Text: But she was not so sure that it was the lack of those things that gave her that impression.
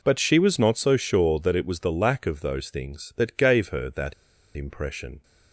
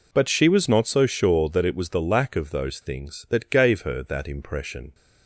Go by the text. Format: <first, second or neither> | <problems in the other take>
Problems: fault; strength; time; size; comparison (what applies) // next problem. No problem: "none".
second | pauses between "that" and "impression"; at 4.1 s; 0.42 s long